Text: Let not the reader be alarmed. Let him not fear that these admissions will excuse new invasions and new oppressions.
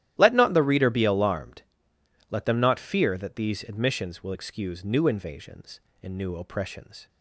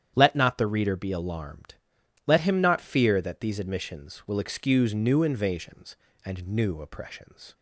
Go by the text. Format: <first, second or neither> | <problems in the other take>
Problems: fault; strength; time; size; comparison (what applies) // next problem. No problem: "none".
second | starts louder than the rest; strong; until 1.1 s; 12.5 dB; strong in the second // says "them" for "him"; at 2.4 s